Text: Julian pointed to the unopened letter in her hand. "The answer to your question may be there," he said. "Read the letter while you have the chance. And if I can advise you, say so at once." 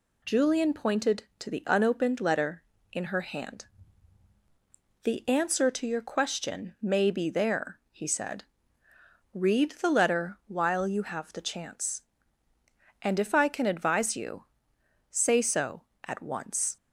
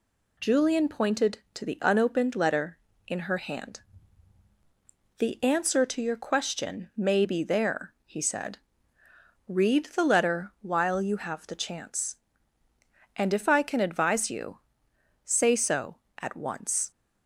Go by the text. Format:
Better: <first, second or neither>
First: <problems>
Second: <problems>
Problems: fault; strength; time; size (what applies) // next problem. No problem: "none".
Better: neither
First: none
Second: none